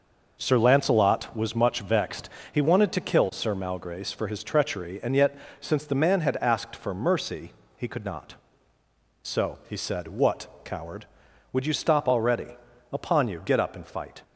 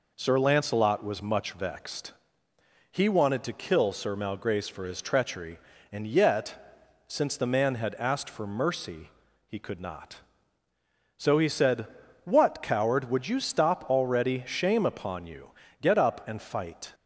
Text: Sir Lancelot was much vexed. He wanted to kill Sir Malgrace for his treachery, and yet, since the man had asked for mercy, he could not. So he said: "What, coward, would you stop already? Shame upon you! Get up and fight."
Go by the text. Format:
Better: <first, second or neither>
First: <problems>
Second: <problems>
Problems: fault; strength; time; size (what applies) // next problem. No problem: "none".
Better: second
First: skips "Shame"; at 12.7 s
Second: none